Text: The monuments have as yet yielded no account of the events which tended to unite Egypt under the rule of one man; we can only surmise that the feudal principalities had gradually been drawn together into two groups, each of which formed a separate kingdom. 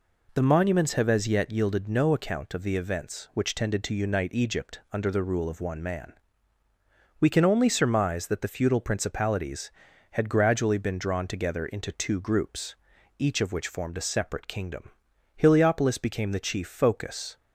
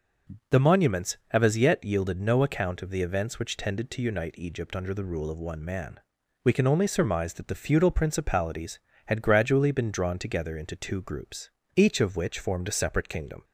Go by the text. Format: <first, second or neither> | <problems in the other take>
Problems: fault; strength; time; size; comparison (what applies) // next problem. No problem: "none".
second | goes on to say "Heliopolis became the chief focus"; strong; from 15.3 s on; 2.0 s long